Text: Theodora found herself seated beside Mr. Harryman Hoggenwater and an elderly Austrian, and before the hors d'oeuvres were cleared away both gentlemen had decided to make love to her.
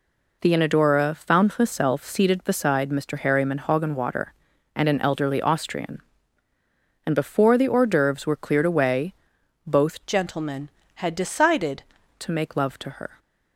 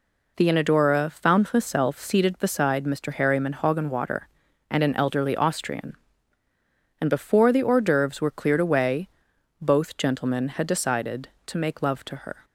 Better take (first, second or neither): second